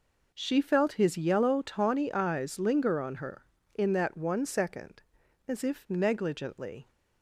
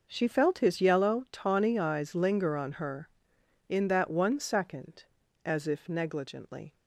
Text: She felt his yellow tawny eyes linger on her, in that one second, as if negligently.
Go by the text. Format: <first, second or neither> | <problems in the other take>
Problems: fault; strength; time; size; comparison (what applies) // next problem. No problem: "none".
neither | none